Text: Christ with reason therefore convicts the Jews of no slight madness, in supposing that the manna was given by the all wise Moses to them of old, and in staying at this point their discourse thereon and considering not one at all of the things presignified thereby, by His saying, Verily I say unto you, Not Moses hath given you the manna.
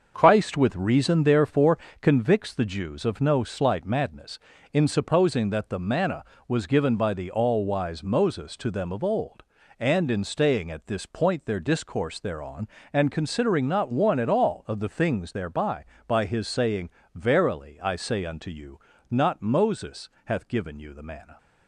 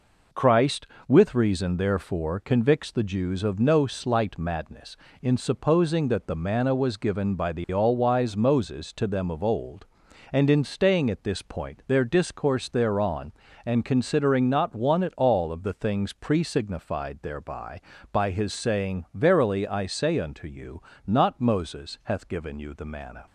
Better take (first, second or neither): second